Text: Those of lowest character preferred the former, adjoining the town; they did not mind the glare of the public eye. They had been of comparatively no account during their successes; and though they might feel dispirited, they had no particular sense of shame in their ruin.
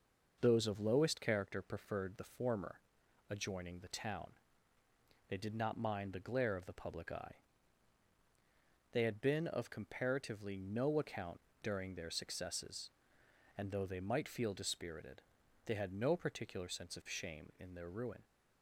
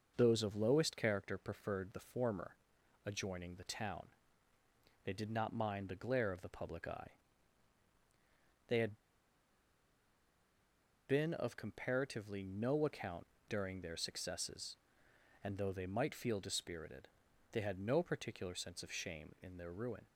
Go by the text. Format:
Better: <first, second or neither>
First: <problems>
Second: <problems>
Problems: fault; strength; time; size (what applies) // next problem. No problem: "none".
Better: first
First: pauses between "account" and "during"; slight; at 11.3 s; 0.24 s long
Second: pauses between "had" and "been"; strong; at 8.9 s; 2.1 s long // pauses between "account" and "during"; slight; at 13.2 s; 0.24 s long